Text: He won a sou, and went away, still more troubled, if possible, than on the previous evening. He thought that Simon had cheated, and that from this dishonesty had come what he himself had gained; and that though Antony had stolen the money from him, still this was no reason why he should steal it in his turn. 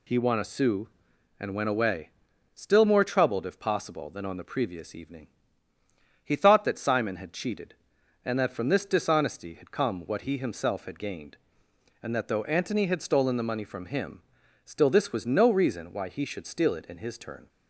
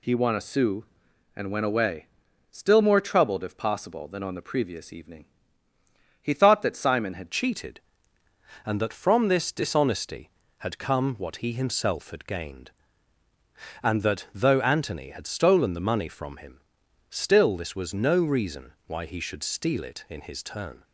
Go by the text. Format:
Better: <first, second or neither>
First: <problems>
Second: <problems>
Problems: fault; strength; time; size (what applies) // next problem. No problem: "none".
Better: first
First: none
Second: changes voice at "cheated"; from 7.3 s on; 13.5 s long